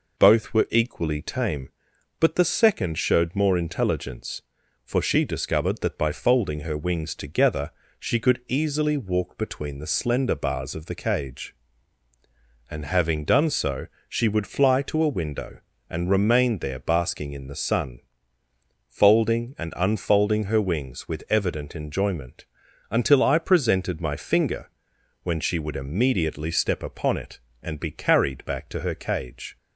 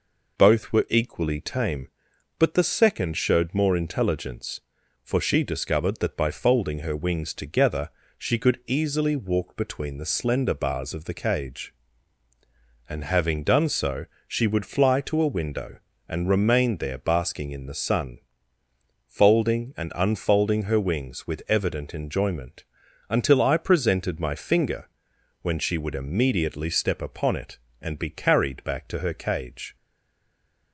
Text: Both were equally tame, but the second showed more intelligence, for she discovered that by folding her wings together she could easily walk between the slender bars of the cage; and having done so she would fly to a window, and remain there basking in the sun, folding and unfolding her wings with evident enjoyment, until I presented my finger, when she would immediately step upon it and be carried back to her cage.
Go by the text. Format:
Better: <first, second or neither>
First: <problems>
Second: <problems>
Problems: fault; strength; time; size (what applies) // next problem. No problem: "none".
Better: first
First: pauses between "together" and "she"; slight; at 7.7 s; 0.28 s long // pauses between "so" and "she"; slight; at 13.8 s; 0.22 s long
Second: pauses between "together" and "she"; slight; at 7.8 s; 0.28 s long // pauses between "so" and "she"; slight; at 14.0 s; 0.22 s long // stays silent after the last word; from 29.7 s on; 1.0 s long